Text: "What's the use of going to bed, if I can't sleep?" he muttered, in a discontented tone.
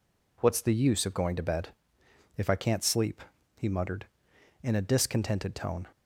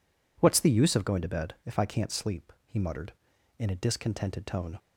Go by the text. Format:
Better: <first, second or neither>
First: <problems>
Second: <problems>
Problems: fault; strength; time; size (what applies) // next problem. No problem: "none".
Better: neither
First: none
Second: none